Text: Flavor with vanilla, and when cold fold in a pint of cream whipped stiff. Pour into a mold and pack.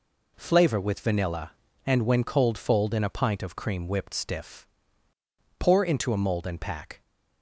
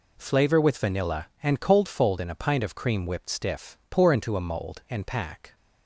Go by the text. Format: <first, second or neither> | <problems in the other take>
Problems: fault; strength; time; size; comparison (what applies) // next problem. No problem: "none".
first | skips "when"; at 1.6 s